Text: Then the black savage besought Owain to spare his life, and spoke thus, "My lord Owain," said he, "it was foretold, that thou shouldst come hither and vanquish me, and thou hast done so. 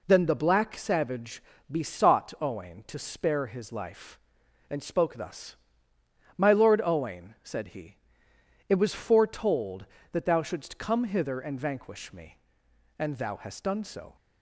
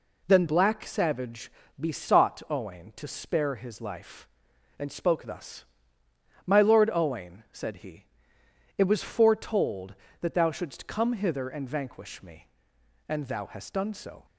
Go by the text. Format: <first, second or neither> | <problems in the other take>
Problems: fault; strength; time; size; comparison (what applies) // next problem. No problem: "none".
first | skips "the"; at 0.4 s // pauses between "savage" and "besought"; slight; at 1.5 s; 0.28 s long; slight in the first